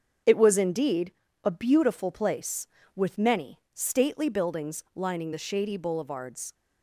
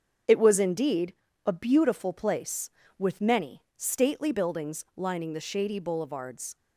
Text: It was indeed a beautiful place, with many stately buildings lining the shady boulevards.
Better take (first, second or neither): neither